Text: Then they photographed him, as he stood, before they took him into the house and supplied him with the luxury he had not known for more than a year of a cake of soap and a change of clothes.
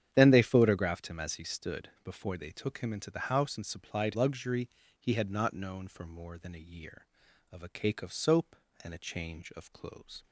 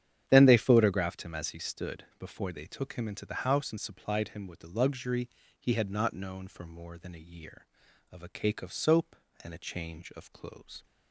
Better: second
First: starts louder than the rest; strong; until 1.1 s; 9.5 dB // skips "him with the"; at 4.1 s // pauses between "luxury" and "he"; slight; at 4.6 s; 0.30 s long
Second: starts louder than the rest; strong; until 1.2 s; 9.5 dB // pauses between "luxury" and "he"; slight; at 5.2 s; 0.30 s long

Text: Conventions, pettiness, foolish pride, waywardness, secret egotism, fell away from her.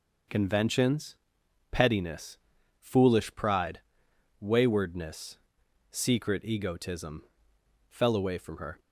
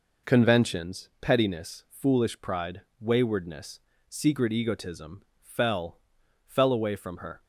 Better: first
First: none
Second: says "fell" twice; at 6.4 s

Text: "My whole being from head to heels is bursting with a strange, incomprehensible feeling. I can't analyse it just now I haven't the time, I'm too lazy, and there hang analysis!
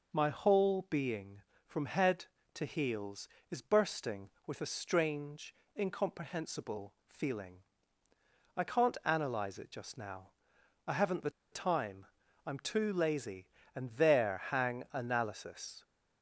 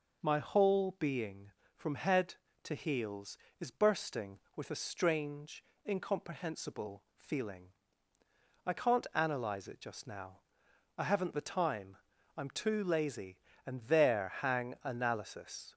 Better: second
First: pauses between "now" and "I"; noticeable; at 10.3 s; 0.56 s long // pauses between "the" and "time"; slight; at 11.2 s; 0.22 s long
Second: pauses between "now" and "I"; noticeable; at 10.4 s; 0.57 s long

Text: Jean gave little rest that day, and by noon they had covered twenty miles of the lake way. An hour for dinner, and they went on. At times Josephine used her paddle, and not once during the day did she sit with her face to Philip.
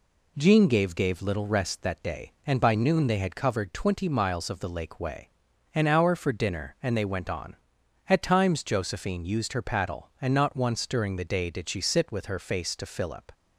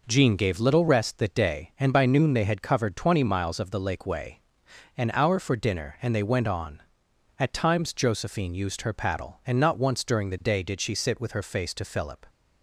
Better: second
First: says "gave" twice; at 0.9 s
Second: none

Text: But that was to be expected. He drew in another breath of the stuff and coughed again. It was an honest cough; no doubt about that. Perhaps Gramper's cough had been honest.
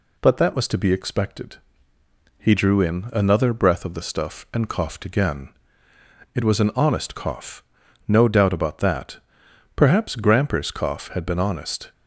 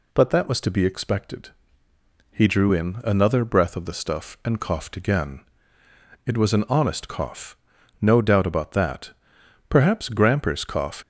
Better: first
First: none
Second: stops before "had been honest"; at 11.0 s

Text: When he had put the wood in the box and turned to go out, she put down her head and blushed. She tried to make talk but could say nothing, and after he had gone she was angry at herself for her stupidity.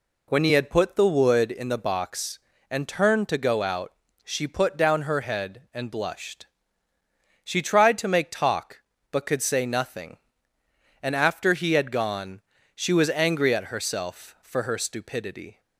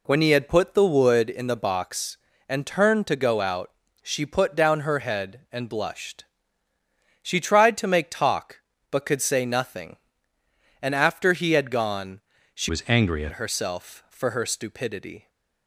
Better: first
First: pauses between "gone" and "she"; slight; at 12.4 s; 0.34 s long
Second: pauses between "gone" and "she"; slight; at 12.2 s; 0.34 s long // changes voice from "was" to "at"; from 12.6 to 13.3 s; 0.7 s long

